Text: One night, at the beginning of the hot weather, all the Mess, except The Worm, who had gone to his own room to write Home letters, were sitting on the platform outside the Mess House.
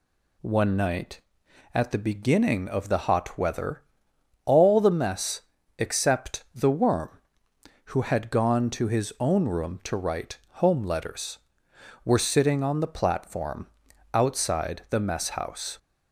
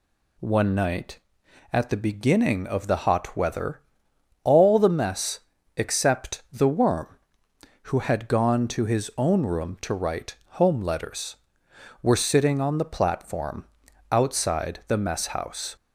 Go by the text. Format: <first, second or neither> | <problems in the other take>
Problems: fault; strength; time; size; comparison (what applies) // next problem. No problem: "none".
neither | pauses between "write" and "Home"; slight; the same in both // pauses between "platform" and "outside"; noticeable; the same in both